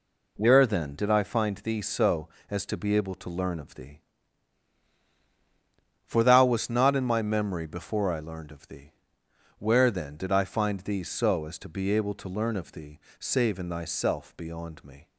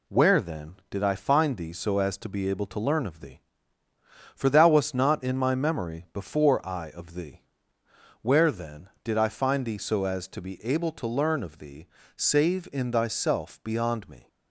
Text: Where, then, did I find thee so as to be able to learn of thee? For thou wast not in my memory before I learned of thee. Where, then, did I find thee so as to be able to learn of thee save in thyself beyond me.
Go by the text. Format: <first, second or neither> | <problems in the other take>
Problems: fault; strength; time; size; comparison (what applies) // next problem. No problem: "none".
first | skips "learned"; at 6.8 s // pauses between "thee" and "save"; slight; at 11.8 s; 0.28 s long; slight in the first